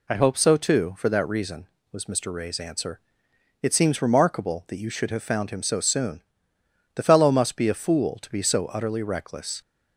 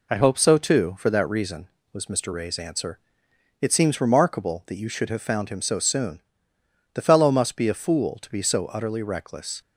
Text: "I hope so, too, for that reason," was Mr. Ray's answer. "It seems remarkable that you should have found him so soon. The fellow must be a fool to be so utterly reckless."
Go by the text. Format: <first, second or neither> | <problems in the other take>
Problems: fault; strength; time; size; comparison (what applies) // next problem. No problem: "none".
first | gets quieter; slight; throughout; 2.5 dB